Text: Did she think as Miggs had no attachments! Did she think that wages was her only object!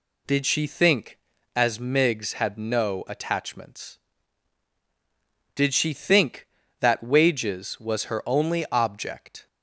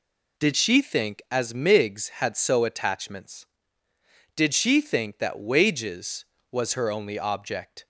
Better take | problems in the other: first | says "so" for "no"; at 2.3 s

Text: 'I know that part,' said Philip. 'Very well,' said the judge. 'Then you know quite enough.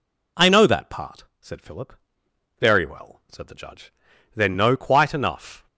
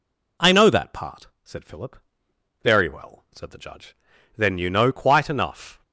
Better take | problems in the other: second | skips "you"; at 4.5 s

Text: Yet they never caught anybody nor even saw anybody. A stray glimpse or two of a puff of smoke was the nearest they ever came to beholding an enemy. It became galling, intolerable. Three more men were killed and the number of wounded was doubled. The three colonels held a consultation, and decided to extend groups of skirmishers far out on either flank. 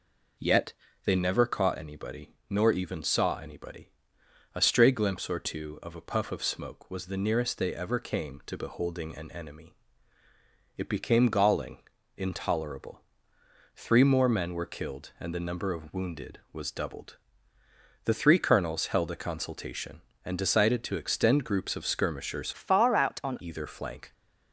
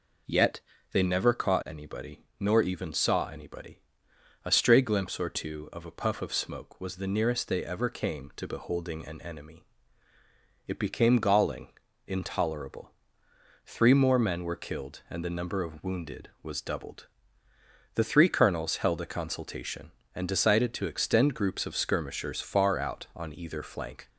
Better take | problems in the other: second | pauses between "Yet" and "they"; slight; at 0.7 s; 0.32 s long; slight in the second // pauses between "anybody" and "nor"; slight; at 2.3 s; 0.16 s long; slight in the second // changes voice from "far" to "on"; from 22.5 to 23.3 s; 0.8 s long

